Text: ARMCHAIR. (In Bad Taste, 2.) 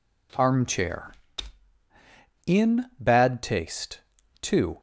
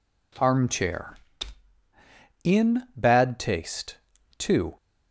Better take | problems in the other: neither | none

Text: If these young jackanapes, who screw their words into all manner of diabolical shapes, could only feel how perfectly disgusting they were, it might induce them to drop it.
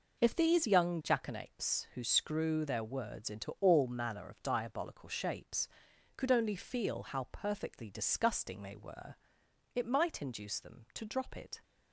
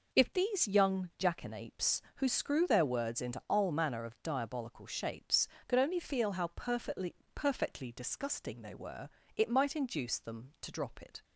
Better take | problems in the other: first | says "perfectly" twice; at 7.3 s

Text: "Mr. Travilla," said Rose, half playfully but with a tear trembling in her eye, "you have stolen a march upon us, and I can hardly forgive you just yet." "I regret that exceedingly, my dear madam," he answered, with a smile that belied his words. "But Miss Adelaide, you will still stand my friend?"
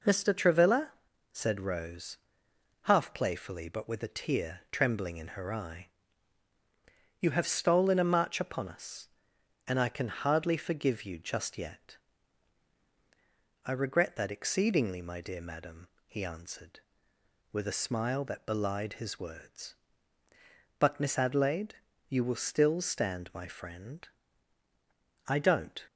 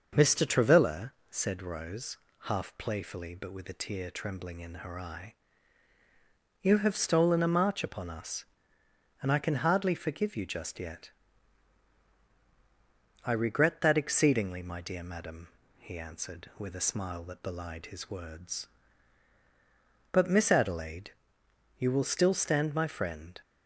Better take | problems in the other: second | goes on to say "I don't"; from 25.2 s on; 0.56 s long

